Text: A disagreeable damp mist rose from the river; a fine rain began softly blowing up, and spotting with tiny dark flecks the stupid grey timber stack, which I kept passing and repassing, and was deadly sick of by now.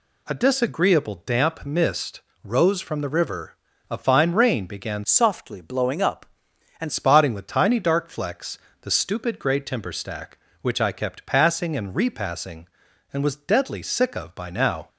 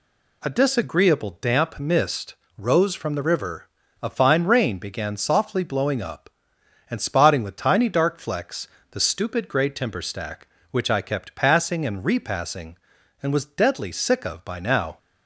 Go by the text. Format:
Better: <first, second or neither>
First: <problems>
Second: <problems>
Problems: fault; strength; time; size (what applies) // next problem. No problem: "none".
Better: second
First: pauses between "mist" and "rose"; slight; at 2.2 s; 0.22 s long // changes voice from "softly" to "and"; from 5.0 to 6.8 s; 1.8 s long // pauses between "flecks" and "the"; slight; at 8.5 s; 0.22 s long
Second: pauses between "mist" and "rose"; slight; at 2.3 s; 0.22 s long // pauses between "flecks" and "the"; slight; at 8.6 s; 0.22 s long